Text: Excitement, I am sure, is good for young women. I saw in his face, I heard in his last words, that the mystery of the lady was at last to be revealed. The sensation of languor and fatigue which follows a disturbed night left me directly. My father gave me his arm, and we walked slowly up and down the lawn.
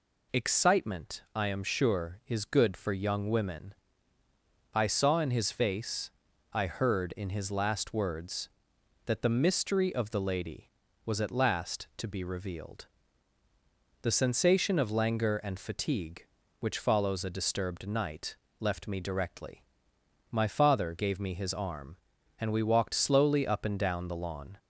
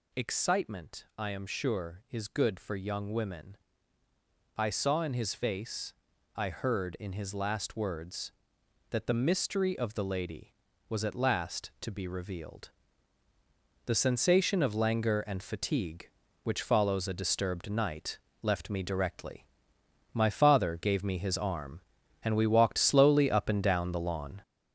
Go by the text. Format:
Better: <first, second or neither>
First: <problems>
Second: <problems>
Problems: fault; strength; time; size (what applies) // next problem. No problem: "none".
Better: first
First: pauses between "night" and "left"; slight; at 18.3 s; 0.24 s long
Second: gets louder; noticeable; throughout; 6 dB // pauses between "night" and "left"; slight; at 18.1 s; 0.24 s long